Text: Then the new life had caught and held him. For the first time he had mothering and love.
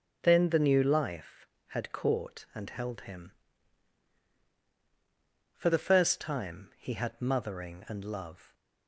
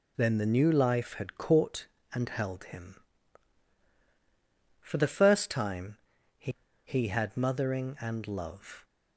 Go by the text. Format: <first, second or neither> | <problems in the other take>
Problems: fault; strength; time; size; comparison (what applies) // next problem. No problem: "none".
first | pauses between "time" and "he"; at 5.9 s; 0.42 s long // says "he" twice; at 6.8 s